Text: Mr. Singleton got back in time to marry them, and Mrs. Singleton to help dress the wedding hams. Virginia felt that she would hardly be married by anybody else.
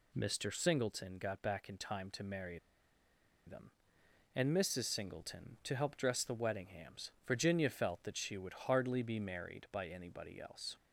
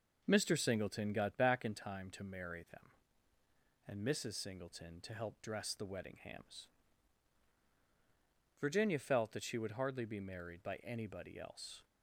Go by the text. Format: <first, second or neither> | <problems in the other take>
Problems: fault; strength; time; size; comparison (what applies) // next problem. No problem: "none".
second | pauses between "marry" and "them"; noticeable; at 2.5 s; 0.88 s long